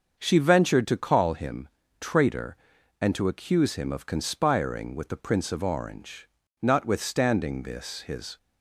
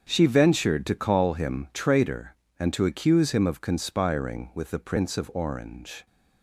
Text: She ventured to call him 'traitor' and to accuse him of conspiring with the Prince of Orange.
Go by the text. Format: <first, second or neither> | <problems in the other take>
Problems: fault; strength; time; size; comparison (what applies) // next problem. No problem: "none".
second | starts louder than the rest; until 1.2 s; 6.5 dB; strong in the second // pauses between "him" and "traitor"; slight; at 1.6 s; 0.32 s long // goes on to say "Notwithstanding this his"; strong; from 6.6 s on; 1.7 s long